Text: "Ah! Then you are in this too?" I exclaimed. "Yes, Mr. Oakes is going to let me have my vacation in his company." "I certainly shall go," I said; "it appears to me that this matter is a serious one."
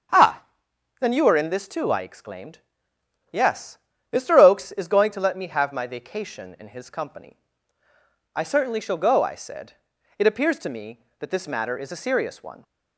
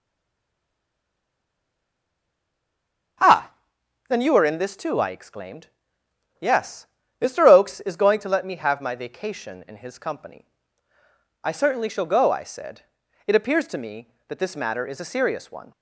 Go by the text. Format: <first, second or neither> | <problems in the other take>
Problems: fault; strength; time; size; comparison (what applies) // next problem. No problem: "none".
first | stays silent before the first word; strong; until 3.1 s; 3.1 s long // starts louder than the rest; strong; until 4.7 s; 7 dB; strong in the first